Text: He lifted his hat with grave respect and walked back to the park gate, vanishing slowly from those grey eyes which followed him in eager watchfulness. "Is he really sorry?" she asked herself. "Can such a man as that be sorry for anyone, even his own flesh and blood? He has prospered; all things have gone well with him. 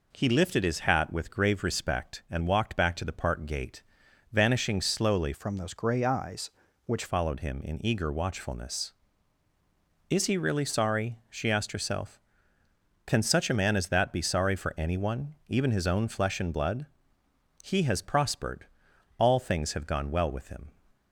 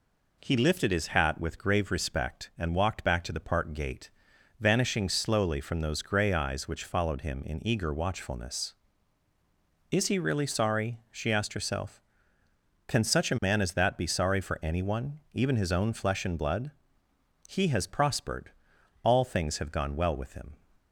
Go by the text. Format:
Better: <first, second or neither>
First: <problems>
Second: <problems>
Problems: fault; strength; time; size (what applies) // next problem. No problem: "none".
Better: second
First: changes voice from "from" to "which"; from 5.3 to 7.0 s; 1.7 s long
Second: none